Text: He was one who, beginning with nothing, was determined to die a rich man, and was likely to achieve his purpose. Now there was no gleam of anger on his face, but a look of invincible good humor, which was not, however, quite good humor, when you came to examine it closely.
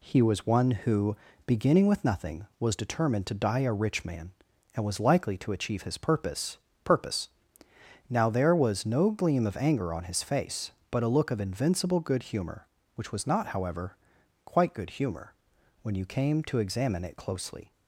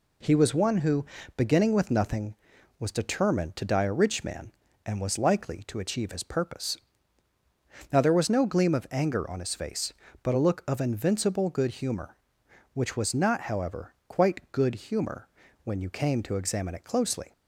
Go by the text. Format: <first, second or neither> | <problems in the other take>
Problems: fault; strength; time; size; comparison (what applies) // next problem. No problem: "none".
second | says "purpose" twice; at 6.8 s